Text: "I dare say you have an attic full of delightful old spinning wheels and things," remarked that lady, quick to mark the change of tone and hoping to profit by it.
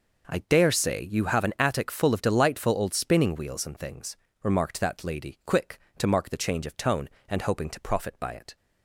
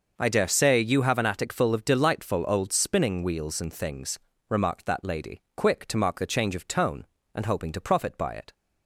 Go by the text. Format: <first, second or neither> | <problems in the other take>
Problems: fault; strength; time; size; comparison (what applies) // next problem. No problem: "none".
neither | none